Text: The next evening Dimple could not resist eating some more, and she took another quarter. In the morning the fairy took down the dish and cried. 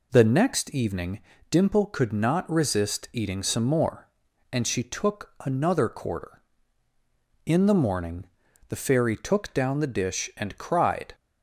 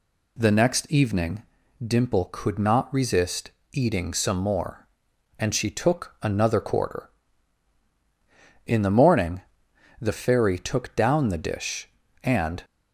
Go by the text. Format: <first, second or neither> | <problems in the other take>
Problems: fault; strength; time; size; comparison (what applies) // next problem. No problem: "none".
first | pauses between "evening" and "Dimple"; at 1.4 s; 0.42 s long; slight in the first // pauses between "resist" and "eating"; slight; at 3.4 s; 0.22 s long // pauses between "morning" and "the"; noticeable; at 9.4 s; 0.58 s long; also in the first // stops before "cried"; at 12.6 s